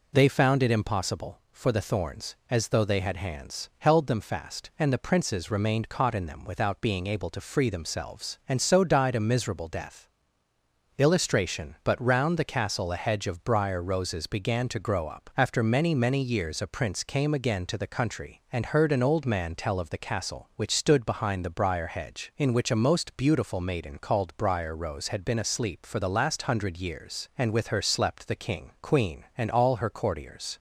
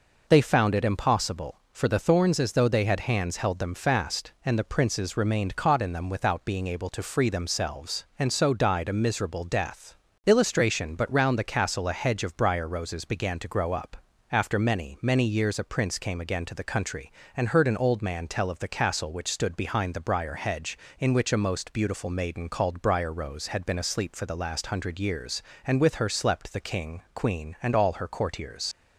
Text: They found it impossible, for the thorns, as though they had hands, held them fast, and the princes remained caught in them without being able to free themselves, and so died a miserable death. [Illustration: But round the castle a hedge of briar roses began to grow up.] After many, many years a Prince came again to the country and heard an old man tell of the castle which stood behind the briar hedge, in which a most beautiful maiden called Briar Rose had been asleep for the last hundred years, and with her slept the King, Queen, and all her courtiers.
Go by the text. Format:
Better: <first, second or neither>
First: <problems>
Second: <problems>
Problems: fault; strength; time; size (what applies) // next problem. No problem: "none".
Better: first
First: none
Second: leaves "courtiers" unfinished; at 28.7 s; 70 ms